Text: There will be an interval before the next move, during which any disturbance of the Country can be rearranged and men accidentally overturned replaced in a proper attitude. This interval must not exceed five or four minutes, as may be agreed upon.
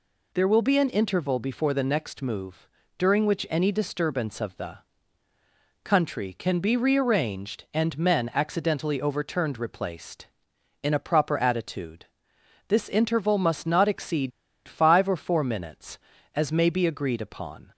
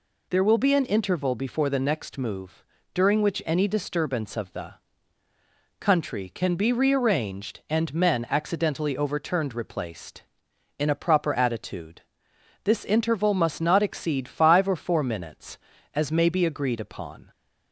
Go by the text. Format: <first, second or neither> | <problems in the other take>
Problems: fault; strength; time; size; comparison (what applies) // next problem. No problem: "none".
second | pauses between "the" and "Country"; at 4.7 s; 1.0 s long; also in the second // pauses between "exceed" and "five"; at 14.3 s; 0.36 s long